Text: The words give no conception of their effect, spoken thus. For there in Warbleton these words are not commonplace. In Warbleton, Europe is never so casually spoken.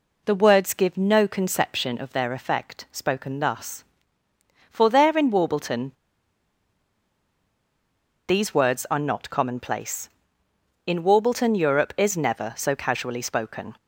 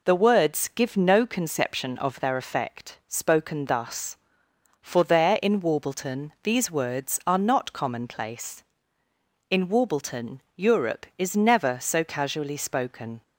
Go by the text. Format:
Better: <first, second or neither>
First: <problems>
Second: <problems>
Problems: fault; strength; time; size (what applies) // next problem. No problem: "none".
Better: second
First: pauses between "Warbleton" and "these"; strong; at 5.9 s; 2.3 s long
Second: none